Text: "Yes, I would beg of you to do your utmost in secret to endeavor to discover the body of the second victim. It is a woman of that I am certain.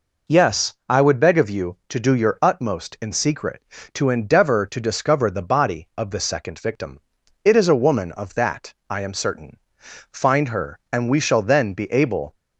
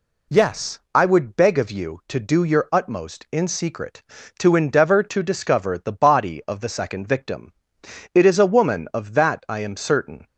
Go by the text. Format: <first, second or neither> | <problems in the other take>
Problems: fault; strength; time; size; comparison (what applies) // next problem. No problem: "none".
second | pauses between "that" and "I"; slight; at 8.7 s; 0.16 s long // goes on to say "Find her and we shall then be able"; strong; from 10.1 s on; 2.2 s long